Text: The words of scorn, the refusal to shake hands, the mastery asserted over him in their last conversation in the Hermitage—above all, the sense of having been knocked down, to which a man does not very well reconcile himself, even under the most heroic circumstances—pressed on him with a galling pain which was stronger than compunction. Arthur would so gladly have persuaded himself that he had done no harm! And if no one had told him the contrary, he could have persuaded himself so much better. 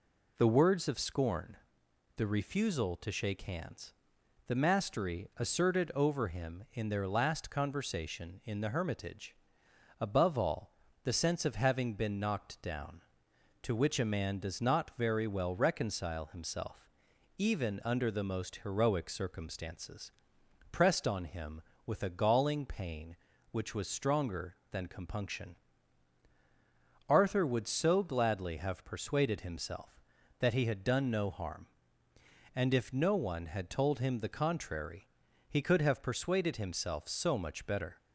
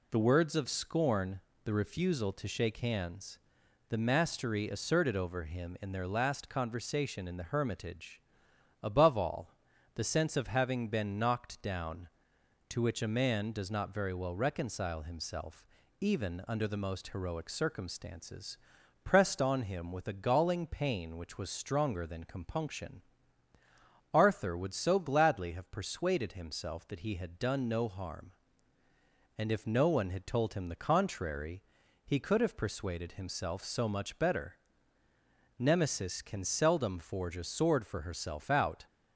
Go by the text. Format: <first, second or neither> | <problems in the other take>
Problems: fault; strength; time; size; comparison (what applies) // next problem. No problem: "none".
first | goes on to say "Nemesis can seldom forge a sword for herself out"; strong; from 35.5 s on; 3.2 s long